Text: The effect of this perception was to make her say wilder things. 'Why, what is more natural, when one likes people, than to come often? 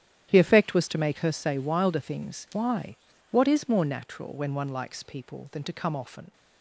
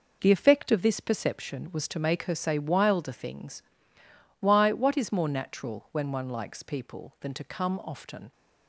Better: second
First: starts louder than the rest; strong; until 1.3 s; 10.5 dB // skips "of this perception"; at 0.7 s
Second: none

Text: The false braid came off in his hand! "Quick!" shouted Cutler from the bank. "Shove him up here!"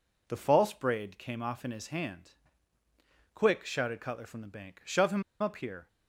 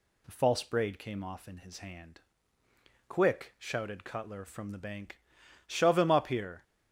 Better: second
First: pauses between "him" and "up"; slight; at 5.2 s; 0.18 s long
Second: none

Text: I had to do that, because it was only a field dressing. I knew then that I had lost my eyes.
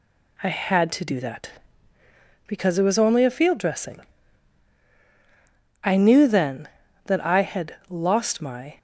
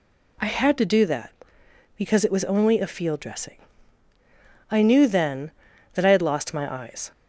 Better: second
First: stops before "eyes"; at 8.7 s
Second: none

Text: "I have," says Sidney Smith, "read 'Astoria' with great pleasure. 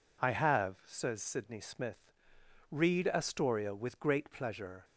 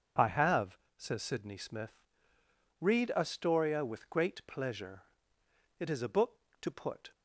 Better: first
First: none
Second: goes on to say "It is a book to put"; from 5.7 s on; 1.3 s long

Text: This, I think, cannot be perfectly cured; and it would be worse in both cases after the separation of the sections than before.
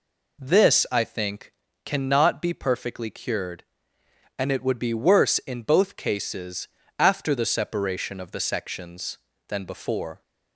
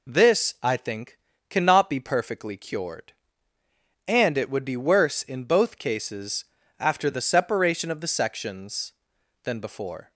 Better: neither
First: pauses between "cases" and "after"; slight; at 6.6 s; 0.32 s long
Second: pauses between "cases" and "after"; slight; at 6.4 s; 0.34 s long

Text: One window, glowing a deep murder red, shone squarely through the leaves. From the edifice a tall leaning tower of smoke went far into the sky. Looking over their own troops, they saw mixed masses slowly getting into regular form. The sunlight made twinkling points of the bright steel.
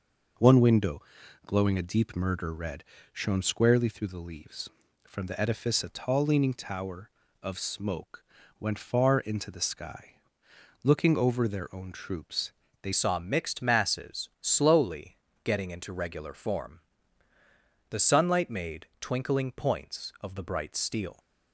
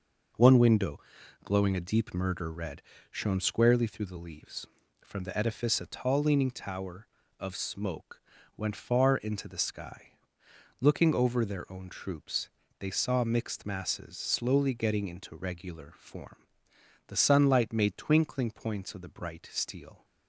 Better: second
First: pauses between "smoke" and "went"; slight; at 8.2 s; 0.36 s long // changes voice at "saw"; from 12.9 s on; 8.2 s long // pauses between "slowly" and "getting"; slight; at 15.1 s; 0.26 s long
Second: pauses between "smoke" and "went"; slight; at 8.2 s; 0.36 s long

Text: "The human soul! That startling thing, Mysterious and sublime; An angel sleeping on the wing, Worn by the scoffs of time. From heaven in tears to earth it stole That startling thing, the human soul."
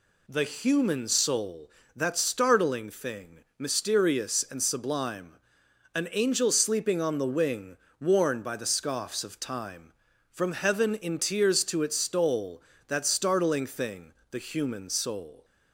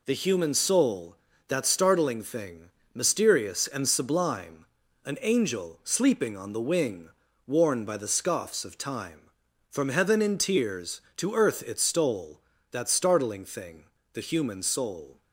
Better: second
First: skips "earth"; at 11.8 s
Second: none

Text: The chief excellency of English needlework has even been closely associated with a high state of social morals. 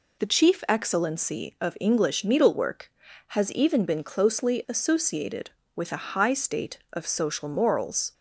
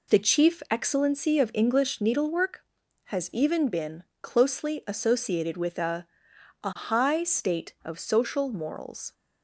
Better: first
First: none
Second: pauses between "been" and "closely"; slight; at 4.0 s; 0.18 s long // says "a" twice; at 6.6 s

